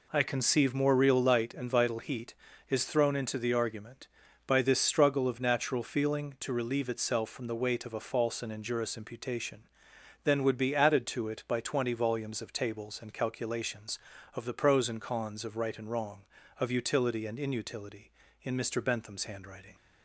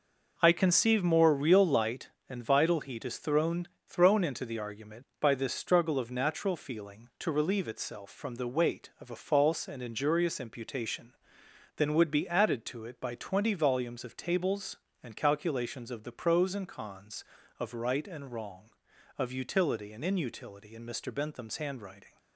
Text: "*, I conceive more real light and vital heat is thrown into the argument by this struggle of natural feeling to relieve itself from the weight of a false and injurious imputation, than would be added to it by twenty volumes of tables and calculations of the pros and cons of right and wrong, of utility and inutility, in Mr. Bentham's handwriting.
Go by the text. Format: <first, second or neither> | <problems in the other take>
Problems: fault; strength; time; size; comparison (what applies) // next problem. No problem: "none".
first | says "thrown" twice; at 3.8 s